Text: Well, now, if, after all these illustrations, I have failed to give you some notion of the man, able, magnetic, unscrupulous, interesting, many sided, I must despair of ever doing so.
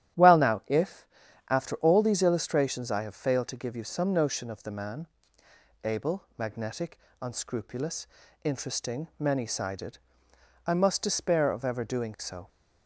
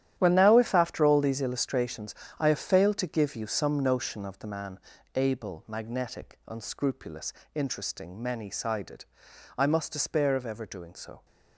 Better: first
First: starts louder than the rest; strong; until 1.6 s; 11 dB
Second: gets quieter; strong; throughout; 12.5 dB // starts louder than the rest; strong; until 1.1 s; 11 dB

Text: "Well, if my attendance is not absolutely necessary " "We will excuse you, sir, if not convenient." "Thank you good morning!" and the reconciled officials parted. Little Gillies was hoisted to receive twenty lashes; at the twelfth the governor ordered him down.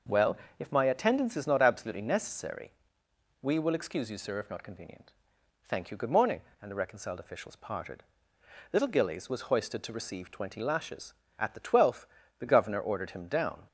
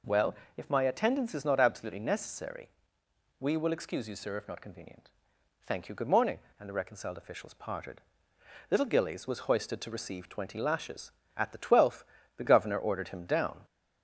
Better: first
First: pauses between "twelfth" and "the"; slight; at 12.0 s; 0.32 s long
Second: gets louder; slight; throughout; 3 dB // pauses between "twelfth" and "the"; slight; at 12.0 s; 0.32 s long

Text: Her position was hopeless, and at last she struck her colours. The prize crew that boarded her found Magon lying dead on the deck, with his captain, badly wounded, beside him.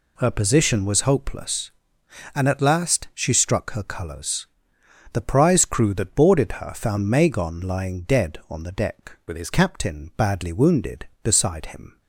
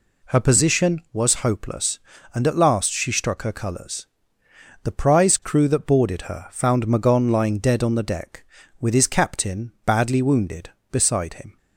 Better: second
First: changes voice from "with" to "his"; from 9.2 to 9.5 s; 0.3 s long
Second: none

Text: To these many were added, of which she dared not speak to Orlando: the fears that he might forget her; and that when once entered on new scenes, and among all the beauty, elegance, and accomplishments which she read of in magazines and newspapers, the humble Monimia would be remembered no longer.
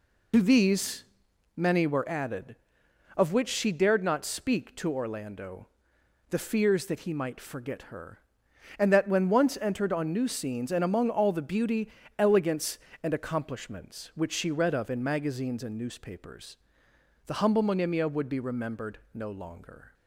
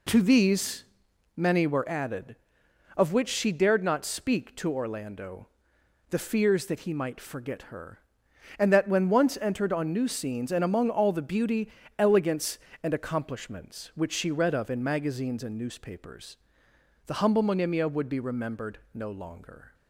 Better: second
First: loses the start of "To"; at 0.3 s; 70 ms // pauses between "these" and "many"; noticeable; at 1.0 s; 0.50 s long // pauses between "remembered" and "no"; slight; at 18.9 s; 0.16 s long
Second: pauses between "these" and "many"; noticeable; at 0.8 s; 0.50 s long // pauses between "remembered" and "no"; slight; at 18.7 s; 0.16 s long

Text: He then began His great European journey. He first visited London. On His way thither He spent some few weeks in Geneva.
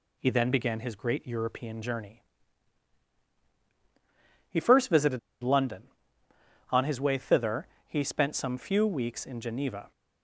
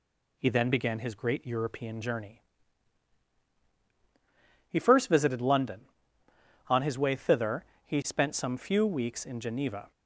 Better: second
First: pauses between "visited" and "London"; slight; at 5.1 s; 0.23 s long // pauses between "thither" and "He"; slight; at 7.6 s; 0.20 s long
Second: pauses between "thither" and "He"; slight; at 7.6 s; 0.20 s long

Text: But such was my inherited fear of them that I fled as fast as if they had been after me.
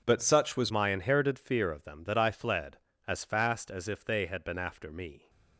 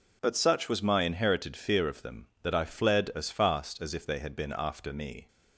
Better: second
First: changes voice at "my"; from 0.7 s on; 4.5 s long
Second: none

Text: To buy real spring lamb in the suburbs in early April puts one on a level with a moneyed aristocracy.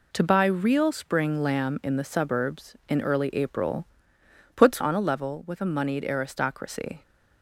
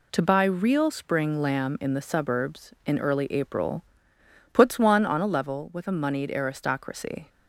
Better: second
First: pauses between "April" and "puts"; noticeable; at 3.8 s; 0.70 s long // skips "one"; at 4.8 s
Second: pauses between "April" and "puts"; noticeable; at 3.8 s; 0.70 s long

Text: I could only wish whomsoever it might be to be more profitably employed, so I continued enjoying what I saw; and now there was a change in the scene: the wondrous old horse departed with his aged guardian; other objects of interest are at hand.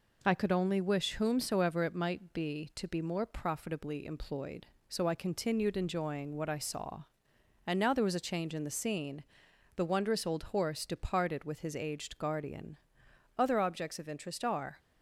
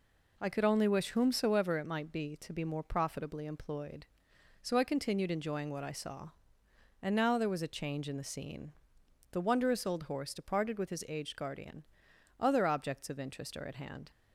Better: second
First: stops before "at hand"; at 14.7 s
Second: none

